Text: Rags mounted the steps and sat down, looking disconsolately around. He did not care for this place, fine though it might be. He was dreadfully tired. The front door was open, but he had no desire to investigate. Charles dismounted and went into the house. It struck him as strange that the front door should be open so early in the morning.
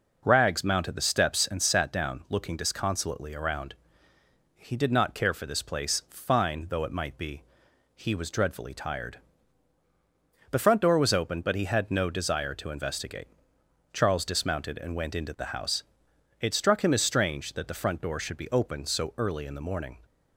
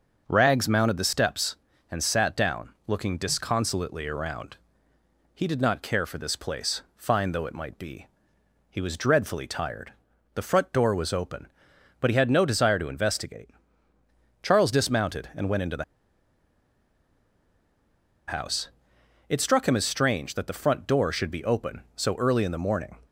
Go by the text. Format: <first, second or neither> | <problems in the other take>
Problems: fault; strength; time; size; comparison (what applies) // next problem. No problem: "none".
first | starts louder than the rest; until 1.2 s; 6.5 dB // pauses between "the" and "house"; strong; at 15.8 s; 2.4 s long